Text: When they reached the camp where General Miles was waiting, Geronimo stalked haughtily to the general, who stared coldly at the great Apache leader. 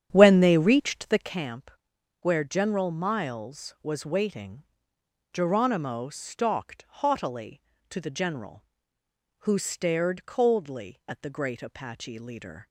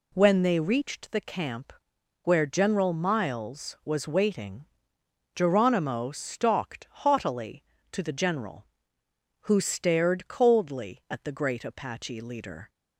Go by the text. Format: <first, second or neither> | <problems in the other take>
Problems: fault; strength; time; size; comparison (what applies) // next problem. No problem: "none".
second | starts louder than the rest; strong; until 1.4 s; 9.5 dB // pauses between "camp" and "where"; noticeable; at 1.7 s; 0.48 s long; noticeable in the second